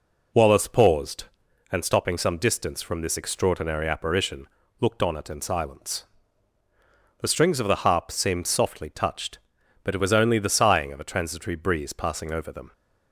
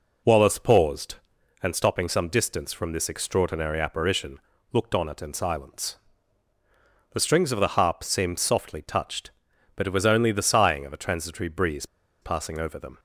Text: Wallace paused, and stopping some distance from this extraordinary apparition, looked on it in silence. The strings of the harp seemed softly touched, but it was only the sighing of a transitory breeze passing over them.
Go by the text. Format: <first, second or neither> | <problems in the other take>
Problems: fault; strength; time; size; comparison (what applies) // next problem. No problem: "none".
first | pauses between "breeze" and "passing"; at 11.8 s; 0.36 s long